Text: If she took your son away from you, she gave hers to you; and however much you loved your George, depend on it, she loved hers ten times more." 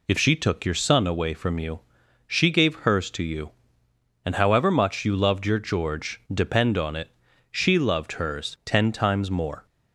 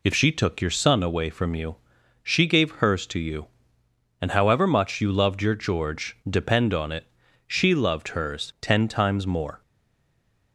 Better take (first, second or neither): first